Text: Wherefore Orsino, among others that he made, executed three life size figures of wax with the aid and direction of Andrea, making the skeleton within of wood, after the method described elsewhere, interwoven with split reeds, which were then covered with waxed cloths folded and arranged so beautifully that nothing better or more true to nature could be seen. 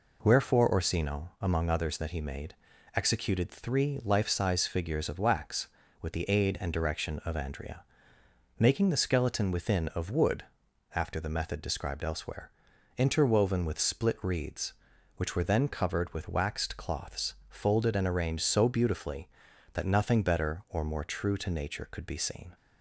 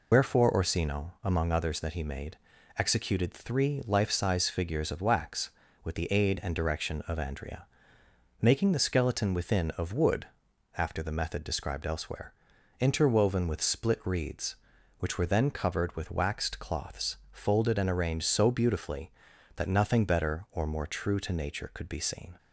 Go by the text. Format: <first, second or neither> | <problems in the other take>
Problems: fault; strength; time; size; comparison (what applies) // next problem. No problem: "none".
first | loses the start of "Wherefore"; at 0.1 s; 90 ms // pauses between "cloths" and "folded"; slight; at 17.1 s; 0.16 s long; slight in the first